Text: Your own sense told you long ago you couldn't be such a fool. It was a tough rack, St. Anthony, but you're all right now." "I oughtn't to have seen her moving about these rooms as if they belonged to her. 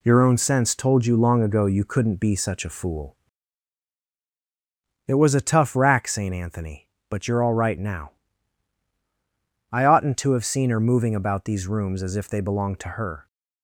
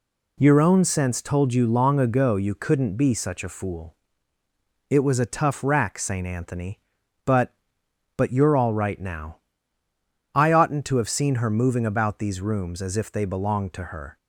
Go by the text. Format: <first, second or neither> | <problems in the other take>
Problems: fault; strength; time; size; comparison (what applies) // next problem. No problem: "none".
first | says "but" twice; at 8.1 s